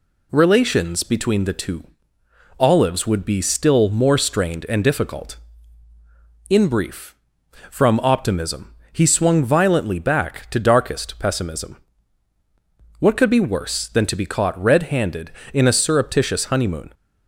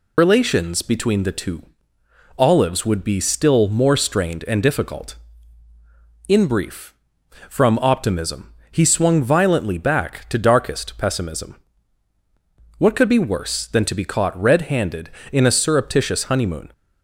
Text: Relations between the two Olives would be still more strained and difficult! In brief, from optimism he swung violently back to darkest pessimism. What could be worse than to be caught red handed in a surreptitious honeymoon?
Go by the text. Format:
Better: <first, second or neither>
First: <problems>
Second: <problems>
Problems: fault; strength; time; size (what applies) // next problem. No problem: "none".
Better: first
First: pauses between "two" and "Olives"; noticeable; at 1.8 s; 0.74 s long // pauses between "optimism" and "he"; slight; at 8.7 s; 0.20 s long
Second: loses the start of "Relations"; at 0.1 s; 90 ms // pauses between "two" and "Olives"; noticeable; at 1.6 s; 0.74 s long // pauses between "optimism" and "he"; slight; at 8.5 s; 0.20 s long